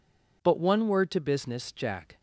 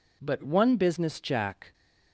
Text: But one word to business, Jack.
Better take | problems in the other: first | skips "word to"; at 0.7 s

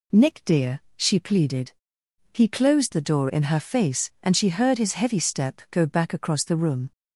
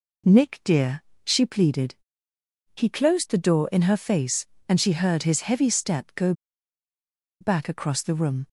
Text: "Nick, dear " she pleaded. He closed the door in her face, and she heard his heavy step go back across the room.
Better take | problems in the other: first | pauses between "go" and "back"; at 6.3 s; 1.0 s long

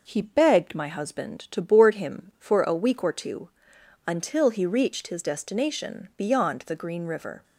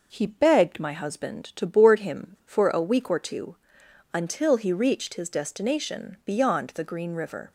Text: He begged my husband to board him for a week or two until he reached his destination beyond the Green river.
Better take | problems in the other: neither | pauses between "two" and "until"; noticeable; the same in both

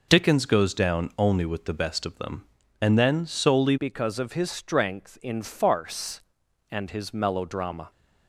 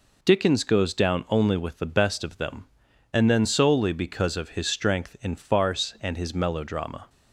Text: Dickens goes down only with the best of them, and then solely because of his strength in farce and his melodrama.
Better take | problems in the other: second | changes voice at "because"; from 3.7 s on; 4.2 s long

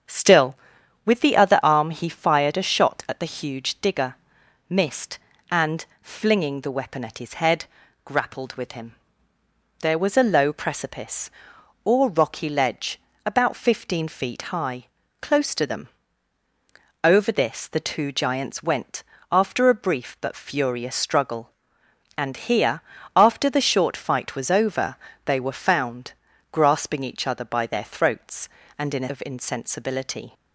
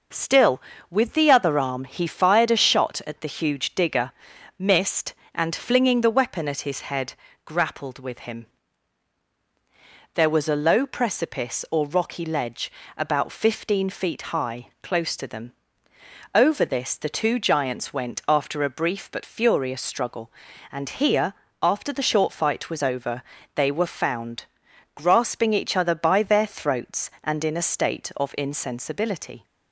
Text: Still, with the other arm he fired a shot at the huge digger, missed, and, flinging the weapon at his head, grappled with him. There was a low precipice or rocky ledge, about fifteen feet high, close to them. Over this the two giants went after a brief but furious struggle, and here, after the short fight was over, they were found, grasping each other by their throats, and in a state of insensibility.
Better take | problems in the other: second | starts louder than the rest; strong; until 1.5 s; 7.5 dB // pauses between "went" and "after"; slight; at 19.0 s; 0.26 s long // skips "state"; at 29.0 s

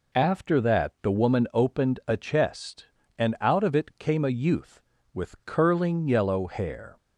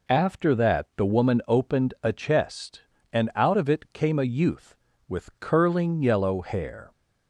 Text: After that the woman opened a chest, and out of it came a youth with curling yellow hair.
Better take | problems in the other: neither | none

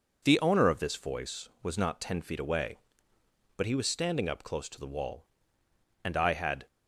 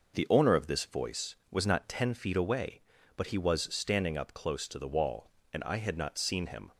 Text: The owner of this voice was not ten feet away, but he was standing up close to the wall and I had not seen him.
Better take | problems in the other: second | stops before "not seen him"; at 6.6 s

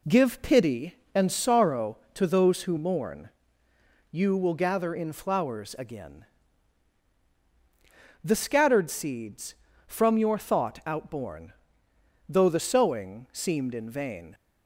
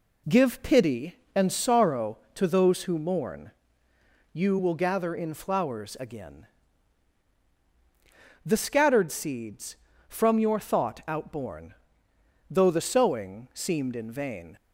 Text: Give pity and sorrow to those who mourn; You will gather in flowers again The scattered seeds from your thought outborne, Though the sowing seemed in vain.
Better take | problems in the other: neither | pauses between "again" and "The"; strong; the same in both

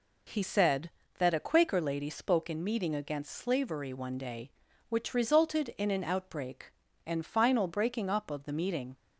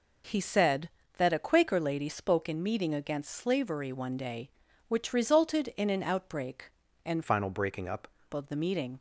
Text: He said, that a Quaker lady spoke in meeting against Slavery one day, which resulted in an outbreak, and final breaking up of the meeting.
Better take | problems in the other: first | changes voice from "final" to "up"; from 7.2 to 8.0 s; 0.8 s long

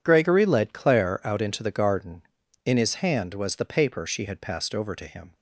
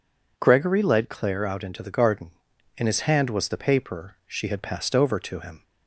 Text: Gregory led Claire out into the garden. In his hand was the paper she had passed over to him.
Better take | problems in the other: neither | none

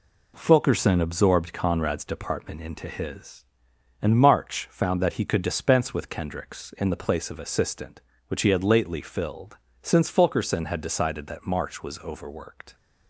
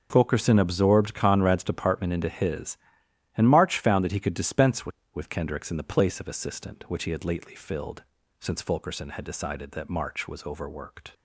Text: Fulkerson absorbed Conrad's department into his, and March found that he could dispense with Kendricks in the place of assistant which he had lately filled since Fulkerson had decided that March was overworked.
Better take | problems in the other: first | starts louder than the rest; until 1.1 s; 6.5 dB // says "with" twice; at 5.1 s // pauses between "filled" and "since"; slight; at 8.0 s; 0.34 s long; slight in the first

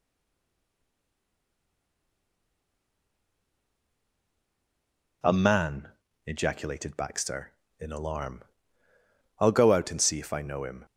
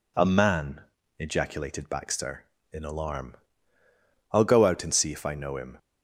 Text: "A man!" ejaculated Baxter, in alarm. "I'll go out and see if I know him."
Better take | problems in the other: second | stays silent before the first word; strong; until 5.2 s; 5.2 s long

